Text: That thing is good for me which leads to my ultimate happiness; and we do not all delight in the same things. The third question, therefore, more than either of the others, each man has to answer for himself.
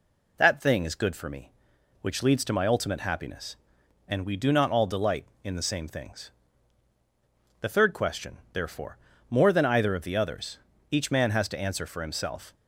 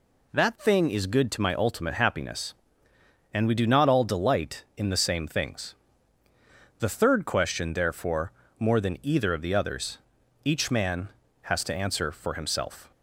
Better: first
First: none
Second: skips "for me which leads"; at 1.3 s

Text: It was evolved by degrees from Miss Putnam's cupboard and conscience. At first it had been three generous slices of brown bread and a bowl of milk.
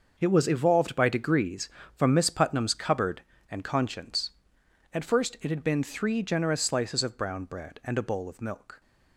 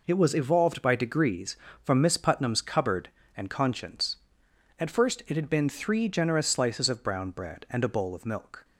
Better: second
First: gets quieter; strong; throughout; 10.5 dB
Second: none

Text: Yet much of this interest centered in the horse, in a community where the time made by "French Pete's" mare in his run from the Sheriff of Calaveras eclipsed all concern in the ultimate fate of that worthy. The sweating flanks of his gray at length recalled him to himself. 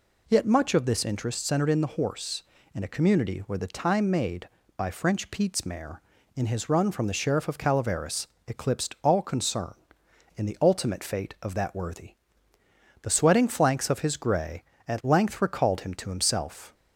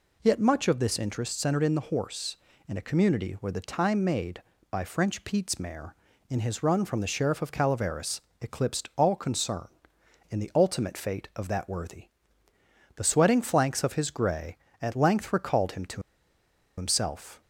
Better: first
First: pauses between "Calaveras" and "eclipsed"; slight; at 8.2 s; 0.20 s long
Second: pauses between "Calaveras" and "eclipsed"; slight; at 8.2 s; 0.20 s long // pauses between "to" and "himself"; noticeable; at 16.0 s; 0.76 s long

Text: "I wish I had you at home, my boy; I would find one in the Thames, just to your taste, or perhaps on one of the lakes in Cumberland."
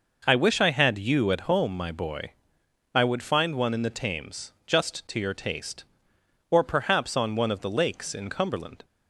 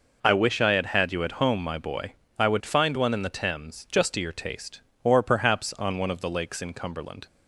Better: first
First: none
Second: says "had" twice; at 0.8 s

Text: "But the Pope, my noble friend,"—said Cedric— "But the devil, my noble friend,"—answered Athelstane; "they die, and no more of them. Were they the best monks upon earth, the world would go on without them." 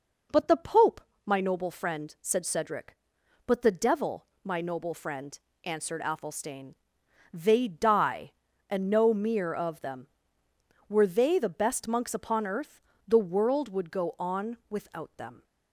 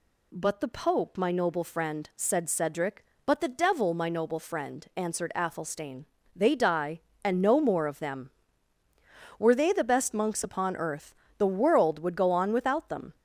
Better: second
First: says "mere" for "more"; at 9.1 s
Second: none

